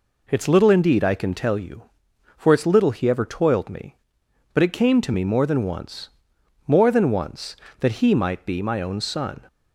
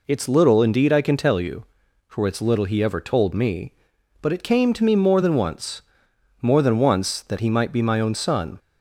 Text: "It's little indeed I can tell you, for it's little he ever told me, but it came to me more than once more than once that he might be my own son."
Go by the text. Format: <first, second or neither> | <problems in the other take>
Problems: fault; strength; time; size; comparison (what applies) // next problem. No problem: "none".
second | says "toiled" for "told"; at 3.2 s // pauses between "once" and "more"; noticeable; at 6.0 s; 0.58 s long; noticeable in the second